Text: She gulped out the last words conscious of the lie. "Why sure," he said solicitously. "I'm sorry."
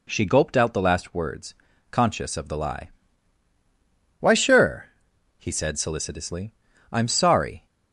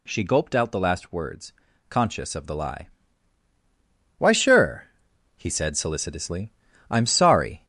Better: first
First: pauses between "words" and "conscious"; at 1.5 s; 0.38 s long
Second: gets louder; noticeable; throughout; 4 dB // pauses between "words" and "conscious"; at 1.5 s; 0.38 s long

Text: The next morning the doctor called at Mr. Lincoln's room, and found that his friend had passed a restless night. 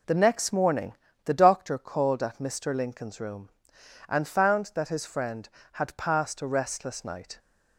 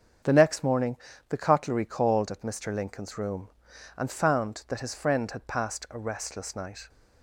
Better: first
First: pauses between "morning" and "the"; slight; at 0.9 s; 0.30 s long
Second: starts louder than the rest; strong; until 1.6 s; 7.5 dB // pauses between "morning" and "the"; slight; at 0.9 s; 0.36 s long // says "cutlery" for "doctor"; at 1.3 s

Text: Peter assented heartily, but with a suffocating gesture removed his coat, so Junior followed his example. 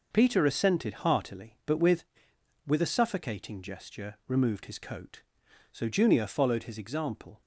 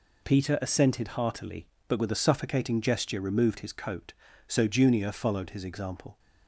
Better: second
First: says "with" twice; at 2.6 s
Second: none

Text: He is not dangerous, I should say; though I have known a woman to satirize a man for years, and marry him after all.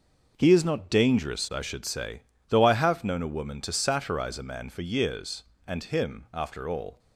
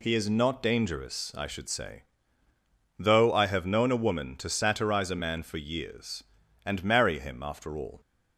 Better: second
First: skips "marry"; at 5.8 s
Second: none

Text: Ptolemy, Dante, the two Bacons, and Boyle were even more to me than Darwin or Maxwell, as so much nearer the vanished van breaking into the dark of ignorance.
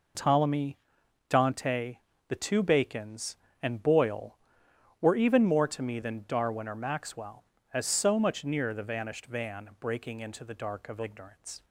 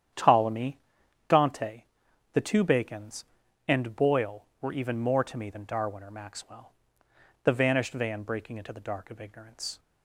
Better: first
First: none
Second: starts louder than the rest; strong; until 1.6 s; 9.5 dB // skips "as so much nearer"; at 7.0 s

